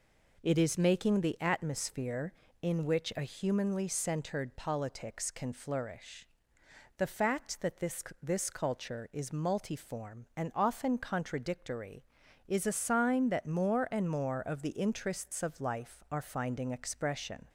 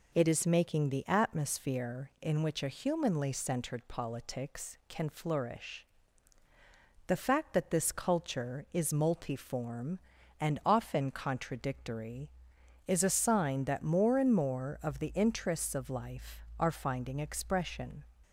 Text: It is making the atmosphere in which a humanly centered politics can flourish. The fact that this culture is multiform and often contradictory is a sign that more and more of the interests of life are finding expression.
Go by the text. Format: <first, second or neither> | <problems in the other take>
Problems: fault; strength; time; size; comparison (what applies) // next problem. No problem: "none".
second | says "this" twice; at 8.2 s